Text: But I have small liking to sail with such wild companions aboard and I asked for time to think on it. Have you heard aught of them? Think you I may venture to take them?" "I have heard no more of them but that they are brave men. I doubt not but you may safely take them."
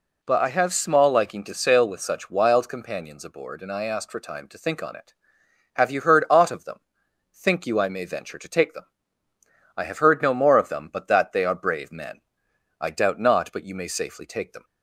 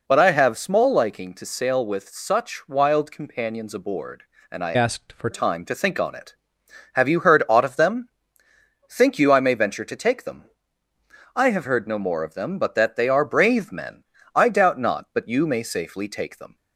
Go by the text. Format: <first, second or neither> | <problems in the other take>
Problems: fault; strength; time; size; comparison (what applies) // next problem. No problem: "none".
first | changes voice from "asked" to "for"; from 4.7 to 5.2 s; 0.5 s long